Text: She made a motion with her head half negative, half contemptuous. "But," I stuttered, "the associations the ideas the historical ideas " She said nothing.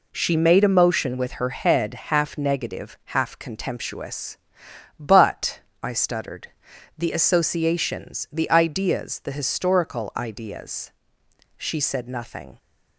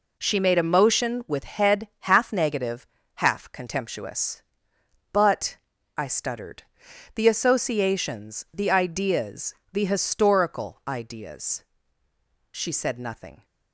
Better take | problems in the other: first | skips "her"; at 1.4 s // pauses between "ideas" and "the"; slight; at 9.5 s; 0.18 s long

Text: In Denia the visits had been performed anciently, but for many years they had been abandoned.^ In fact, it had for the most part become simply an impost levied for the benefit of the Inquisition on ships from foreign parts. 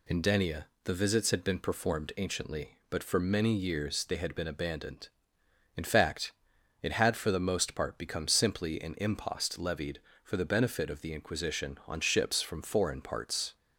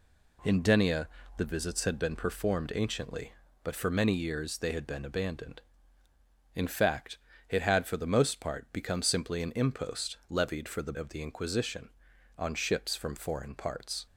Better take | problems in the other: first | pauses between "Denia" and "the"; slight; at 1.0 s; 0.28 s long; slight in the first // skips "benefit"; at 10.9 s

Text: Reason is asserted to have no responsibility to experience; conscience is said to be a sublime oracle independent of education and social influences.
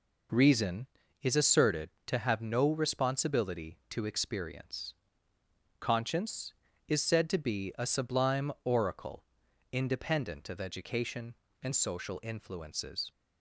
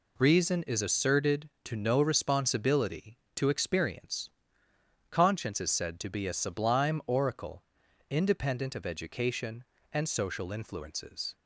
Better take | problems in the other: first | skips "have"; at 1.7 s // pauses between "oracle" and "independent"; noticeable; at 7.6 s; 0.46 s long; noticeable in the first

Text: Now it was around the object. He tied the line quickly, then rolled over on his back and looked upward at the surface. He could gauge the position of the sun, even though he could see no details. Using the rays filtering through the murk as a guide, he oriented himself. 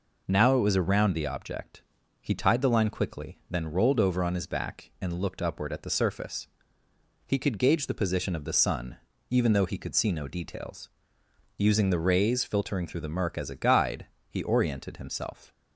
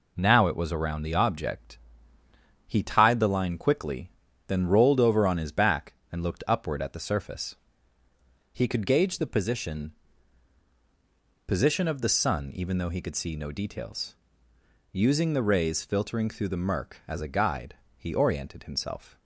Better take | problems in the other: first | says "position" twice; at 11.4 s

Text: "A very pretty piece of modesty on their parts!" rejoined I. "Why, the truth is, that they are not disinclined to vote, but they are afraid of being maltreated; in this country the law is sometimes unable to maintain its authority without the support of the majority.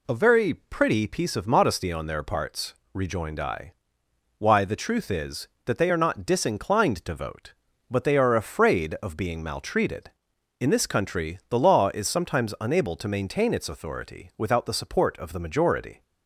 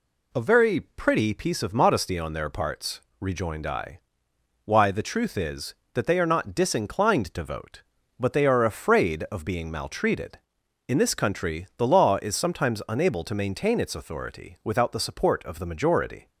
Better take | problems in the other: neither | none

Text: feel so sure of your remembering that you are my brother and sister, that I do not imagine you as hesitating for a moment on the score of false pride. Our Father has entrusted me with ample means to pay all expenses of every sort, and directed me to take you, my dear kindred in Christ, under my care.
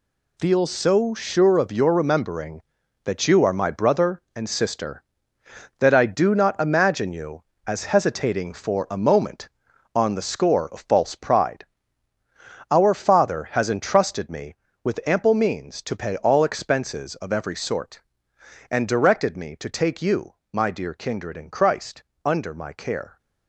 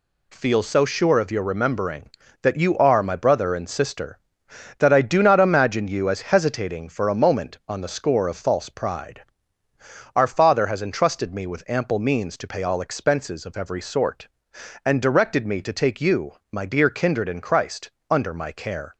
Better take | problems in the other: second | gets quieter; strong; throughout; 9 dB

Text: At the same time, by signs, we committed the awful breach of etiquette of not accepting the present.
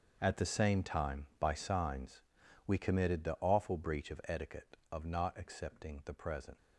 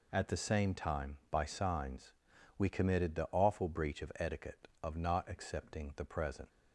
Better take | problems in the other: second | gets quieter; strong; throughout; 14 dB

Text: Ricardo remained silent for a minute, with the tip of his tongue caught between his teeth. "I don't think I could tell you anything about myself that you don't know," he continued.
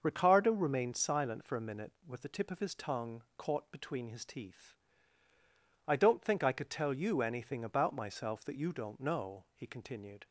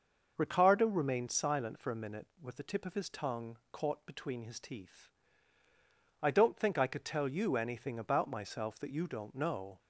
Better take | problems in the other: first | starts louder than the rest; until 1.3 s; 6 dB; also in the first // pauses between "tongue" and "caught"; slight; at 3.5 s; 0.16 s long; slight in the first // stops before "he continued"; at 9.7 s

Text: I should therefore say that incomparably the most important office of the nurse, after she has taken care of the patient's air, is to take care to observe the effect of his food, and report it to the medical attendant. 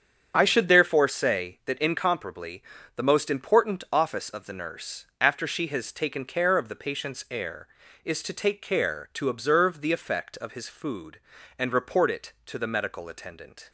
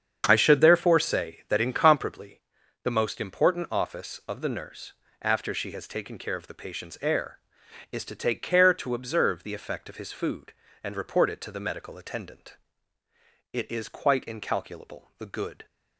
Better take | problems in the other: first | starts louder than the rest; strong; until 1.2 s; 7.5 dB; strong in the first // pauses between "incomparably" and "the"; at 2.4 s; 0.40 s long; slight in the first // goes on to say "It is quite incalculable the good"; strong; from 13.5 s on; 2.1 s long

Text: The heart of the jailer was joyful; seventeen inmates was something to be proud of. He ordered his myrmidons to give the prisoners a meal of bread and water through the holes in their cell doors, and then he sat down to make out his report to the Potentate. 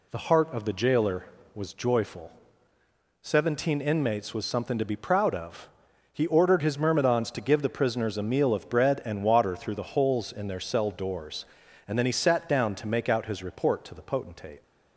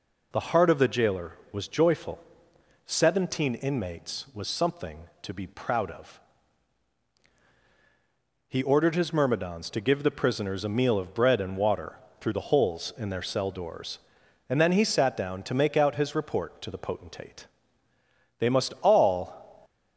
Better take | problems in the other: first | pauses between "water" and "through"; slight; at 11.9 s; 0.20 s long // goes on to say "They must all"; noticeable; from 18.3 s on; 1.2 s long

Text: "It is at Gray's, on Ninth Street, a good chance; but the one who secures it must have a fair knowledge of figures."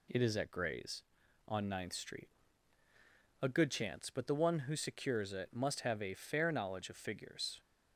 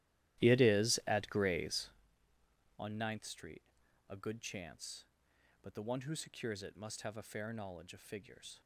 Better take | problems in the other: first | starts louder than the rest; strong; until 2.1 s; 14 dB

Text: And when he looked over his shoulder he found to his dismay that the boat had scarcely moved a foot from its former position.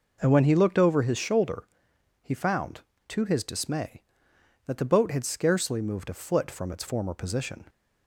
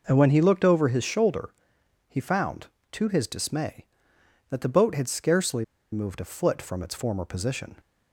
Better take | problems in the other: first | pauses between "shoulder" and "he"; noticeable; at 1.4 s; 0.58 s long; noticeable in the first // pauses between "scarcely" and "moved"; slight; at 5.6 s; 0.28 s long

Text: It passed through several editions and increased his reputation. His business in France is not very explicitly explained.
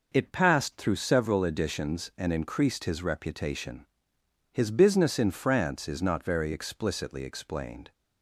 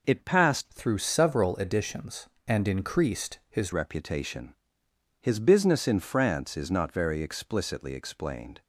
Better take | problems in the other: first | changes voice from "through" to "his"; from 0.6 to 3.7 s; 3.1 s long

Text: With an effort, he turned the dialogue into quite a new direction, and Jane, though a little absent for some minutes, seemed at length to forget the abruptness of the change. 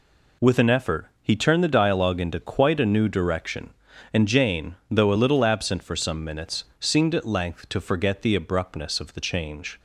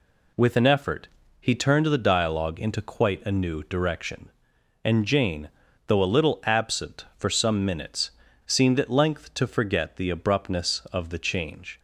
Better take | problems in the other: neither | none

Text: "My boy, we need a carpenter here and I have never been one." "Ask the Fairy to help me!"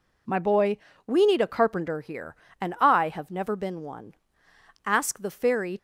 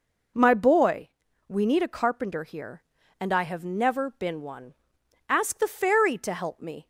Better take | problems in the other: second | stops before "to help me"; at 5.7 s

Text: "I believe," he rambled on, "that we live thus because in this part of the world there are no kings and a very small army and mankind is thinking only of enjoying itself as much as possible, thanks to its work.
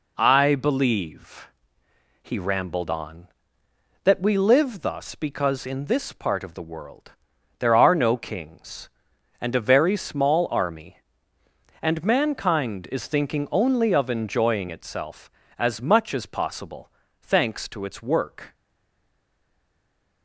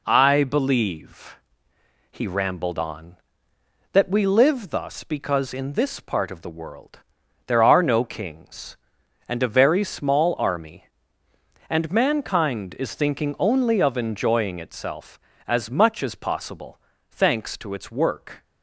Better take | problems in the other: second | pauses between "world" and "there"; noticeable; at 7.1 s; 0.48 s long; noticeable in the second // stays silent after the last word; noticeable; from 18.5 s on; 1.7 s long

